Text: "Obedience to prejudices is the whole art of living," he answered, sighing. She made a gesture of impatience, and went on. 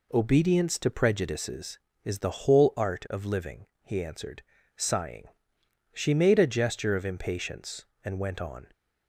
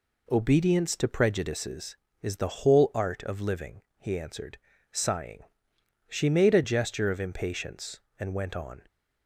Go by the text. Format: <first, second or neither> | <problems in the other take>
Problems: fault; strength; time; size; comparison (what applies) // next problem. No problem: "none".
neither | none